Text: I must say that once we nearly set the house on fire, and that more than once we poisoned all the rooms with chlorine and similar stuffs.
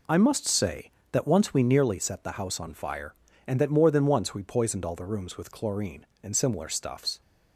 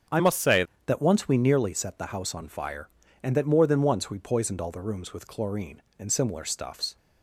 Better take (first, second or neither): first